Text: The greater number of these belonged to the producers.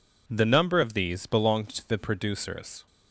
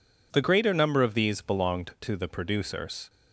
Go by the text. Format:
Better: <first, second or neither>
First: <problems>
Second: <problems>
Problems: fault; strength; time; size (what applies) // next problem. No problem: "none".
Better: second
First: skips "greater"; at 0.4 s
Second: none